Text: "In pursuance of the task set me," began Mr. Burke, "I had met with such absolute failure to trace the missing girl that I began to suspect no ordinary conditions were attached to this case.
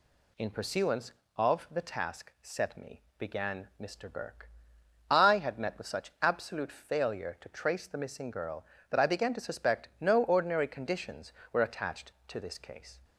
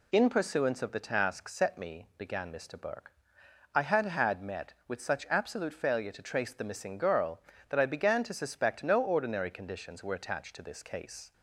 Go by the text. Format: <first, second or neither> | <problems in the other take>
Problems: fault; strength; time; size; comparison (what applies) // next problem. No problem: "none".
first | says "had" twice; at 4.0 s